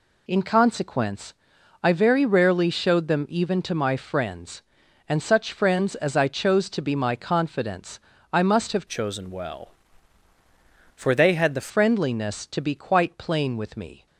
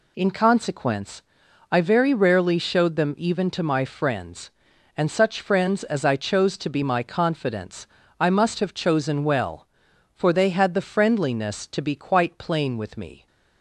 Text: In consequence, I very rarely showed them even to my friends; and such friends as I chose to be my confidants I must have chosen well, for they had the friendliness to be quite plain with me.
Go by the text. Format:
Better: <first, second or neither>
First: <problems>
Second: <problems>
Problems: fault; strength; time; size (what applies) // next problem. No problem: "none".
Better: second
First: pauses between "confidants" and "I"; slight; at 8.0 s; 0.32 s long // changes voice from "chosen" to "the"; from 8.8 to 11.6 s; 2.8 s long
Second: pauses between "confidants" and "I"; slight; at 7.8 s; 0.32 s long